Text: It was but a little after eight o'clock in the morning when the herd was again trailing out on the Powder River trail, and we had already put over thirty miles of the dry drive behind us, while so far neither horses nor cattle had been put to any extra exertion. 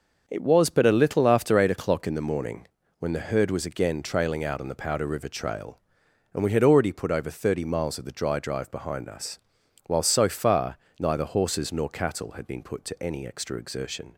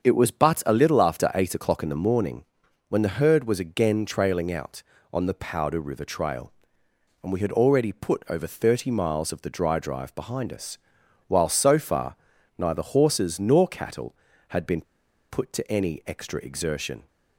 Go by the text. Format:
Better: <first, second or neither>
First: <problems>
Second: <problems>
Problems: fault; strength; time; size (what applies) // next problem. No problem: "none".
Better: first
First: pauses between "morning" and "when"; slight; at 2.6 s; 0.32 s long // pauses between "far" and "neither"; slight; at 10.7 s; 0.20 s long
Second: starts louder than the rest; strong; until 1.0 s; 7 dB // pauses between "morning" and "when"; at 2.4 s; 0.44 s long // pauses between "far" and "neither"; at 12.1 s; 0.42 s long // pauses between "been" and "put"; noticeable; at 14.8 s; 0.47 s long